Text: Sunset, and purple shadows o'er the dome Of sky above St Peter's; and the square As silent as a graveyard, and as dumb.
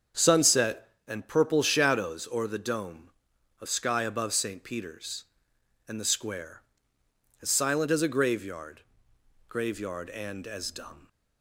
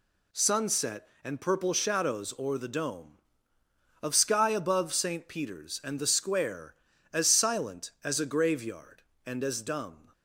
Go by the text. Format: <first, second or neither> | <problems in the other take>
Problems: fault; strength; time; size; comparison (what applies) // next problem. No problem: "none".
second | starts louder than the rest; until 1.3 s; 7 dB // says "graveyard" twice; at 9.4 s